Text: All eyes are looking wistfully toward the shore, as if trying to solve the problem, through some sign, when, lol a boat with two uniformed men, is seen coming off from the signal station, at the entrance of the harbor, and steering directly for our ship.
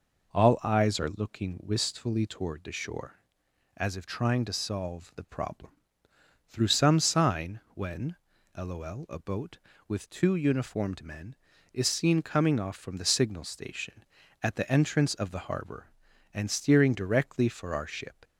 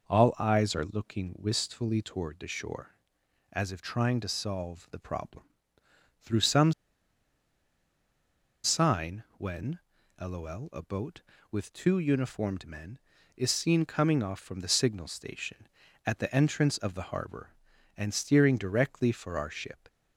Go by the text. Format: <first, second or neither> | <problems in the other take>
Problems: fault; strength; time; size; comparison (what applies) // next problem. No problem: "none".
first | pauses between "some" and "sign"; strong; at 6.7 s; 1.9 s long